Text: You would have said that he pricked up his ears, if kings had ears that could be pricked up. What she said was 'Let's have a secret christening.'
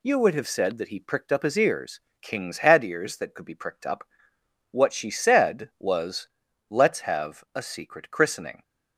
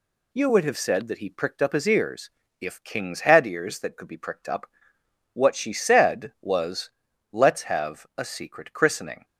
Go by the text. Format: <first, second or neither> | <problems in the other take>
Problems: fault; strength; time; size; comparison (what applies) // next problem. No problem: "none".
second | skips "if"; at 2.1 s // pauses between "was" and "Let's"; at 6.2 s; 0.42 s long; also in the second